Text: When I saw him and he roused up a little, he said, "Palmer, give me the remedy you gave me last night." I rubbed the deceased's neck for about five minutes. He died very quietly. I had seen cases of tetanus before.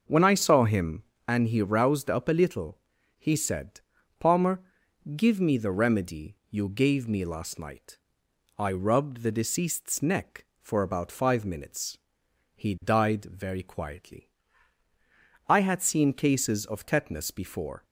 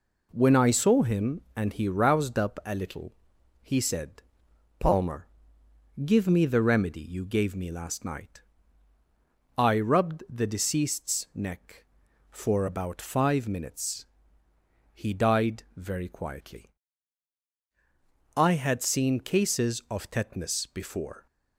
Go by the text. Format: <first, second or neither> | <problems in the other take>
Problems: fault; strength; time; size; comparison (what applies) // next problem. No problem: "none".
second | starts louder than the rest; until 1.4 s; 6 dB // pauses between "remedy" and "you"; slight; at 6.3 s; 0.16 s long